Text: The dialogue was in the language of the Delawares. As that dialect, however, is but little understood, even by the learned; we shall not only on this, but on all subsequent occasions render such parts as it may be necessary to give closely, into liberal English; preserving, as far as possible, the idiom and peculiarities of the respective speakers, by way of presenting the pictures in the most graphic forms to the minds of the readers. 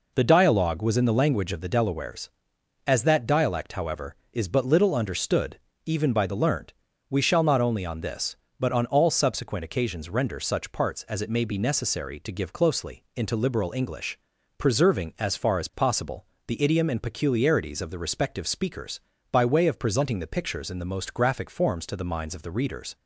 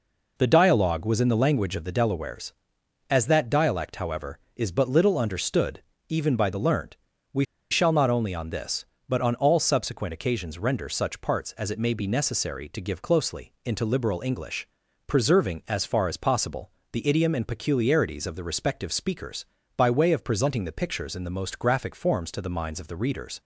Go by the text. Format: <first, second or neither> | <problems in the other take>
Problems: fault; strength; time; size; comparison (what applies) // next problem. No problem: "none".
first | pauses between "we" and "shall"; slight; at 7.4 s; 0.28 s long